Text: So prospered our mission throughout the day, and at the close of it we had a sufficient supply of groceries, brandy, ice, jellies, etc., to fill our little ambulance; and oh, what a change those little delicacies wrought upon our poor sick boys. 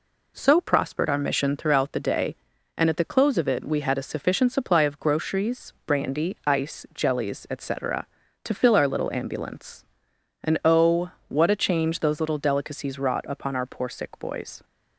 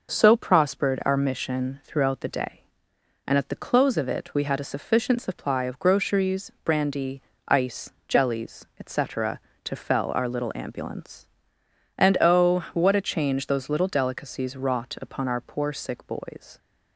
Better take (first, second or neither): first